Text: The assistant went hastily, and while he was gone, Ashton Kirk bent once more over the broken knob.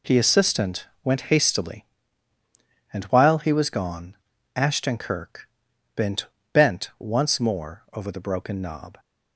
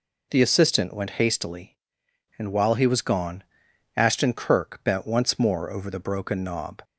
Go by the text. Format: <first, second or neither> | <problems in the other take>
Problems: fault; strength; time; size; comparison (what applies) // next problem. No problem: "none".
second | pauses between "assistant" and "went"; slight; at 0.8 s; 0.18 s long // pauses between "Kirk" and "bent"; noticeable; at 5.4 s; 0.48 s long // says "bent" twice; at 6.5 s